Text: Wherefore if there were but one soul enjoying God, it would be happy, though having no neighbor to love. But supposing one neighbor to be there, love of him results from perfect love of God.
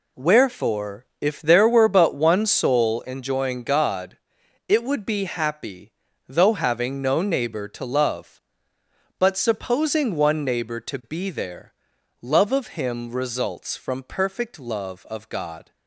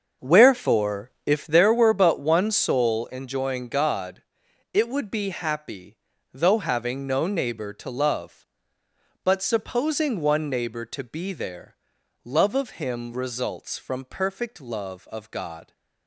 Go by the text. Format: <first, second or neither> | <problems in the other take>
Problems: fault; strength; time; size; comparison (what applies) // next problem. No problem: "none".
first | starts louder than the rest; until 1.6 s; 6.5 dB